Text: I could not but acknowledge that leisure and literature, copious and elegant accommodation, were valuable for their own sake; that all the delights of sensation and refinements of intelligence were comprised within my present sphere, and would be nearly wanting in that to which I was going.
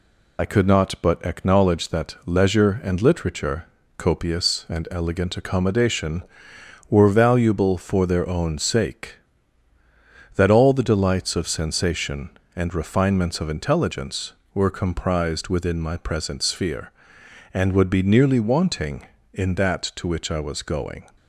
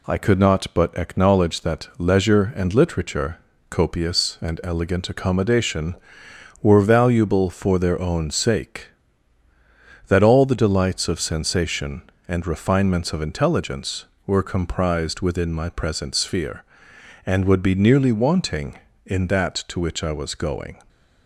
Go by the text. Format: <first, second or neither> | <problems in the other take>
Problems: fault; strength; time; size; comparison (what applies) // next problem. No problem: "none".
second | loses the start of "I"; at 0.3 s; 55 ms